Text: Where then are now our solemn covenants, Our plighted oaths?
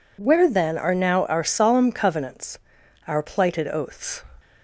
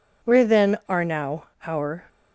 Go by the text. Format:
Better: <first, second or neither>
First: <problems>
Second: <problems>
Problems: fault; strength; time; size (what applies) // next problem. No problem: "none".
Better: first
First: none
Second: pauses between "now" and "our"; slight; at 1.4 s; 0.20 s long // stops before "solemn covenants Our plighted oaths"; at 2.0 s